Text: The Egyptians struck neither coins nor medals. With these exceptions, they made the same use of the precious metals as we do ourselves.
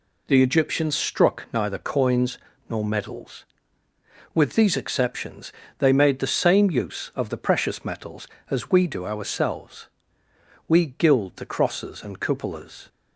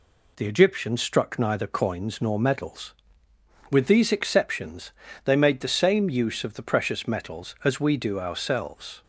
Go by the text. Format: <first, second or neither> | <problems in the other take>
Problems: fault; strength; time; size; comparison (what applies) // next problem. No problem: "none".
second | pauses between "coins" and "nor"; slight; at 2.3 s; 0.30 s long // goes on to say "We gild the crosses and cupolas"; strong; from 10.6 s on; 2.2 s long